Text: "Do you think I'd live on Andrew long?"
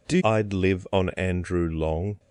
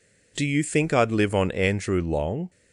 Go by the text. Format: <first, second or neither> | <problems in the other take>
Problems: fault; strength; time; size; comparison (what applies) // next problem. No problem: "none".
second | skips "you think"; at 0.1 s